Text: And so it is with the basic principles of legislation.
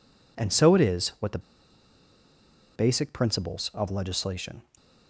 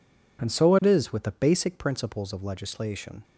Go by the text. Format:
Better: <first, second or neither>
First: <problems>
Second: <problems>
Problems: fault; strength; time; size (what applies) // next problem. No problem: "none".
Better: second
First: pauses between "the" and "basic"; strong; at 1.3 s; 1.3 s long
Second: none